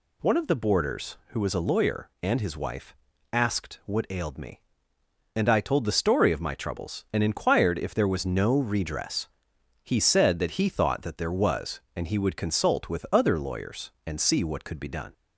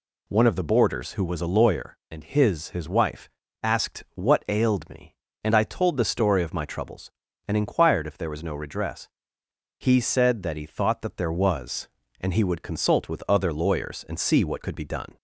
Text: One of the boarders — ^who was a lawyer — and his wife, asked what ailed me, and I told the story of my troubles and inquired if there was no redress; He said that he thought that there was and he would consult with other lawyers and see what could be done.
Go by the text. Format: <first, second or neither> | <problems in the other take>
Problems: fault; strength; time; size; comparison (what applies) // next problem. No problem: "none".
first | says "his" twice; at 2.6 s